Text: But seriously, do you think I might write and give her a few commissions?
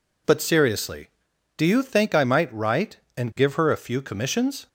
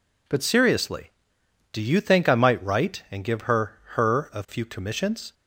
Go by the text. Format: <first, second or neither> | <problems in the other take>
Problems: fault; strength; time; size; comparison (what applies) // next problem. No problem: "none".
first | says "her" twice; at 3.9 s